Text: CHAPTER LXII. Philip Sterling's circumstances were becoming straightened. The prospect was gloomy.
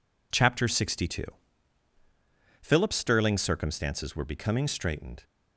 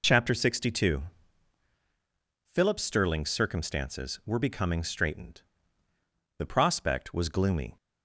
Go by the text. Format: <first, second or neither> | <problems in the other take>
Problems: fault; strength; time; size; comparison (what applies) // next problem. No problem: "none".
second | stops before "The prospect was gloomy"; at 5.2 s